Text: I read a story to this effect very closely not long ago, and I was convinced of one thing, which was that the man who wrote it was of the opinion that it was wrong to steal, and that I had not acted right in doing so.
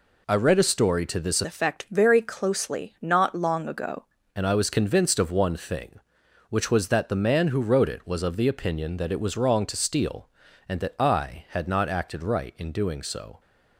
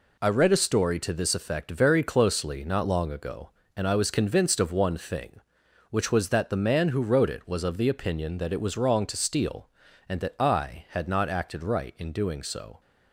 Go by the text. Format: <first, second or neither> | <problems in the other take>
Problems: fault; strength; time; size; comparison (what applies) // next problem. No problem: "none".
second | changes voice from "effect" to "ago"; from 1.4 to 4.0 s; 2.6 s long